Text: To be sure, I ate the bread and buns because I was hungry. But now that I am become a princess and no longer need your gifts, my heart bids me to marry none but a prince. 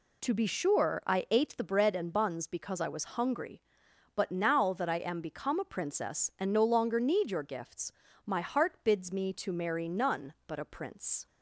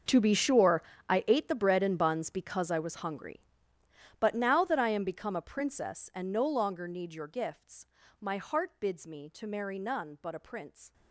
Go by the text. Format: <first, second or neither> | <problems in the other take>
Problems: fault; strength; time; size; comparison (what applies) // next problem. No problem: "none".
first | gets quieter; strong; throughout; 18 dB